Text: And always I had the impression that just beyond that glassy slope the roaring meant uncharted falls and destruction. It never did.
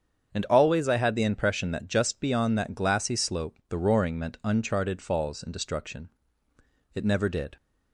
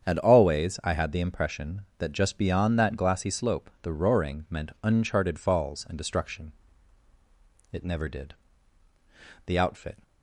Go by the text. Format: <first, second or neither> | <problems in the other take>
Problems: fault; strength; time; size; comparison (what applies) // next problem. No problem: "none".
first | starts louder than the rest; strong; until 1.0 s; 8 dB; strong in the first // goes on to say "The outfit"; from 9.4 s on; 0.56 s long